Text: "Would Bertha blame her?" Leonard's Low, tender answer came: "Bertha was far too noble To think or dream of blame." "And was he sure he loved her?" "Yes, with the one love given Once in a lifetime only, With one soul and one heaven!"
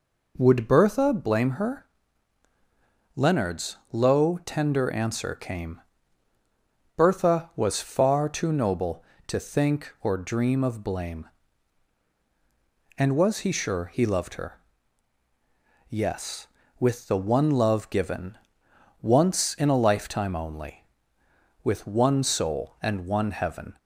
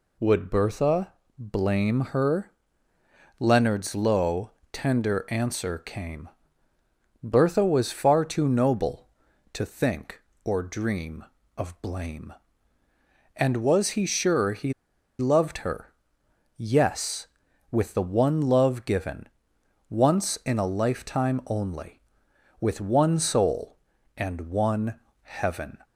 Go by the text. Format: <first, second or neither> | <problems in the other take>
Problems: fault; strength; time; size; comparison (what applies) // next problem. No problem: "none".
first | pauses between "Bertha" and "blame"; slight; at 1.1 s; 0.24 s long // pauses between "he" and "loved"; noticeable; at 14.7 s; 0.46 s long // pauses between "given" and "Once"; noticeable; at 19.2 s; 0.62 s long; noticeable in the first // pauses between "one" and "heaven"; slight; at 24.9 s; 0.26 s long